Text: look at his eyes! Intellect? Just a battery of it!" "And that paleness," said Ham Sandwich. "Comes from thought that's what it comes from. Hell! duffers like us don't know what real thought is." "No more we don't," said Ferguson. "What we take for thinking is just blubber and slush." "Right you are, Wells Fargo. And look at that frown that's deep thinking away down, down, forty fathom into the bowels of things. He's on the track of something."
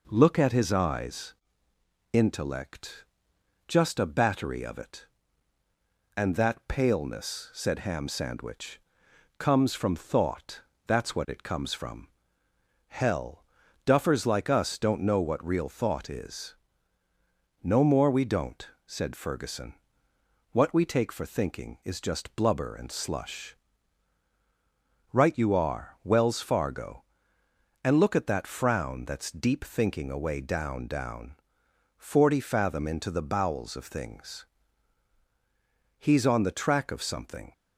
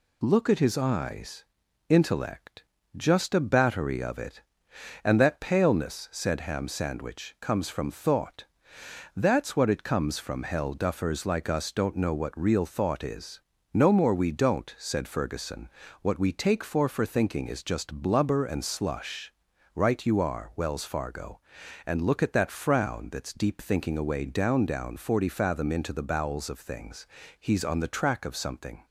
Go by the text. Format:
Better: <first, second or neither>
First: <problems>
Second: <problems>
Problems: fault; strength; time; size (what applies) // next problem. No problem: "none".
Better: first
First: pauses between "thought" and "that's"; slight; at 10.6 s; 0.24 s long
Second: pauses between "thought" and "that's"; noticeable; at 8.4 s; 0.72 s long // says "for" twice; at 16.8 s